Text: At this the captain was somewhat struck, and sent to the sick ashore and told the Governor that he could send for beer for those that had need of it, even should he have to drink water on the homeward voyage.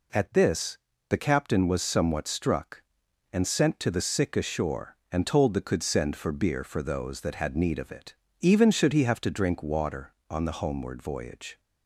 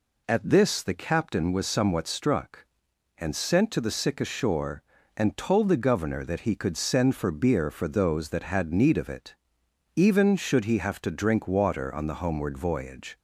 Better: second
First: pauses between "this" and "the"; slight; at 0.7 s; 0.30 s long // skips "Governor that he"; at 5.5 s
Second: none

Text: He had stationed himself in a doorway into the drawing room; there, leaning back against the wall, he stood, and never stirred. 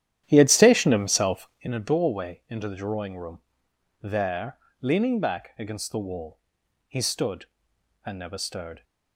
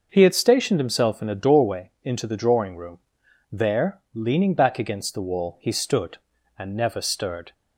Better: second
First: starts louder than the rest; strong; until 1.7 s; 11 dB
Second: none

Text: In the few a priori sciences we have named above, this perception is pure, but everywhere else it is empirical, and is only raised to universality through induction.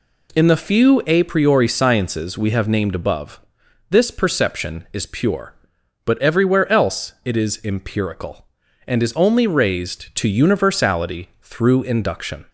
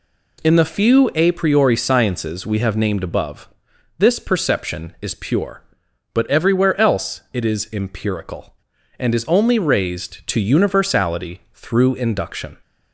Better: neither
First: none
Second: none

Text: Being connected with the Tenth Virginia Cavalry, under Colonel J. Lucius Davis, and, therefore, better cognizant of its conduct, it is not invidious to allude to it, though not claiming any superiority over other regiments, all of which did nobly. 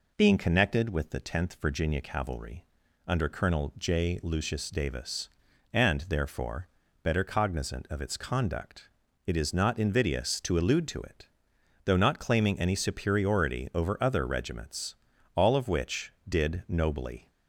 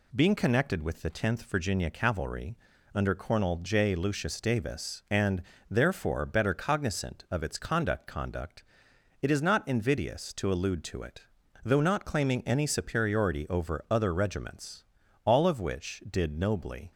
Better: first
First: none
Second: says "conduct" twice; at 8.0 s

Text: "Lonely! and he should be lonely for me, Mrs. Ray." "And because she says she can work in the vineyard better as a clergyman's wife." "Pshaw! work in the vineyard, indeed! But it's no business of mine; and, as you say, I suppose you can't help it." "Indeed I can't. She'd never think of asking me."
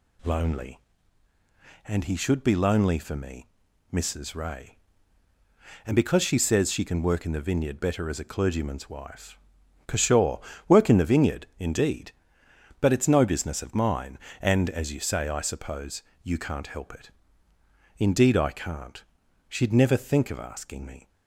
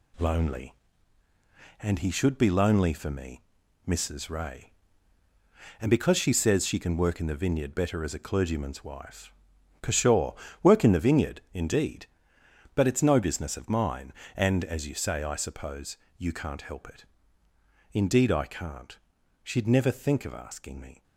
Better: first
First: pauses between "suppose" and "you"; slight; at 16.0 s; 0.20 s long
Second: gets quieter; noticeable; throughout; 5.5 dB // pauses between "suppose" and "you"; slight; at 15.9 s; 0.20 s long

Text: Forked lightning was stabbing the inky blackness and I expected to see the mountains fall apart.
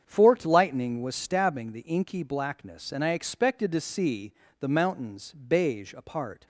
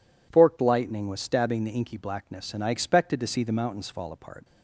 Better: second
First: starts louder than the rest; strong; until 1.0 s; 7.5 dB // pauses between "see" and "the"; slight; at 4.3 s; 0.26 s long // says "beige" for "fall"; at 5.3 s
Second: none

